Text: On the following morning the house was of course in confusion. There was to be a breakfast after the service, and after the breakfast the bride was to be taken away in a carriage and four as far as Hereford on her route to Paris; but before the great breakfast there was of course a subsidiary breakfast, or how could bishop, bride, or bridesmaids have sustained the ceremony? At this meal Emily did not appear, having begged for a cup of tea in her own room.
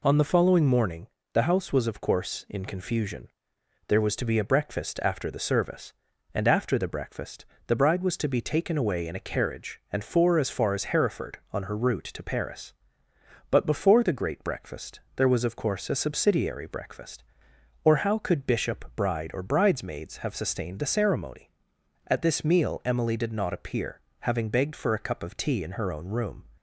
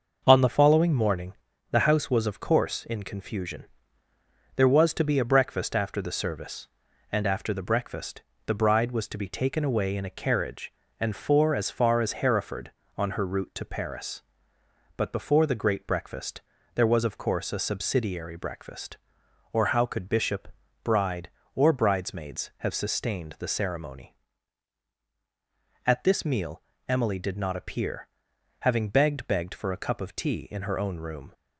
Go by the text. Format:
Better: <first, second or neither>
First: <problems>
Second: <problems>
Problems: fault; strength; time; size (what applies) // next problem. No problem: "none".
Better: first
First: pauses between "morning" and "the"; slight; at 1.0 s; 0.24 s long // pauses between "breakfast" and "the"; slight; at 7.4 s; 0.22 s long // pauses between "breakfast" and "there"; slight; at 14.9 s; 0.16 s long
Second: starts louder than the rest; noticeable; until 1.2 s; 6 dB // pauses between "morning" and "the"; at 1.3 s; 0.40 s long // pauses between "breakfast" and "the"; slight; at 8.2 s; 0.24 s long // pauses between "breakfast" and "there"; slight; at 16.4 s; 0.34 s long // pauses between "meal" and "Emily"; slight; at 26.6 s; 0.26 s long // says "begged" twice; at 29.2 s